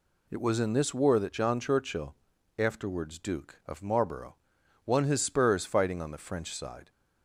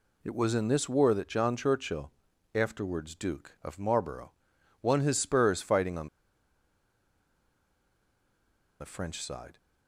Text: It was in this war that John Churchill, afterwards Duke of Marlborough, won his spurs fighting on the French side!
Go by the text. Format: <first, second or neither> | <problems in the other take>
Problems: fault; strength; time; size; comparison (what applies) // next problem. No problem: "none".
first | pauses between "on" and "the"; strong; at 6.0 s; 2.7 s long